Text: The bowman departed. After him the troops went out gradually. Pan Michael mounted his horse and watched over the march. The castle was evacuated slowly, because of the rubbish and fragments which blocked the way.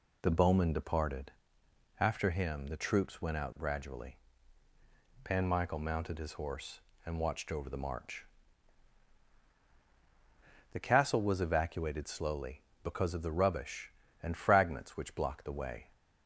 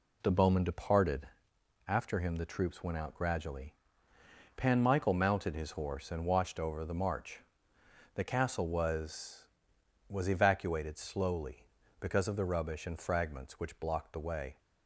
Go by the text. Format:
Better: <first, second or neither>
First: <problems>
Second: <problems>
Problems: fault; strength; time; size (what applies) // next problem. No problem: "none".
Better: first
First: none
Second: says "was" twice; at 10.0 s